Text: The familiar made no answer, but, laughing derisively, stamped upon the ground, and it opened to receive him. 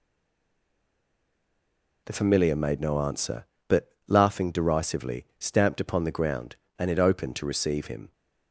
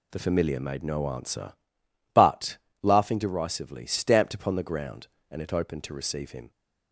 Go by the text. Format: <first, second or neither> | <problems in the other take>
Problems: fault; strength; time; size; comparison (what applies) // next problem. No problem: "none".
second | stays silent before the first word; noticeable; until 2.0 s; 2.0 s long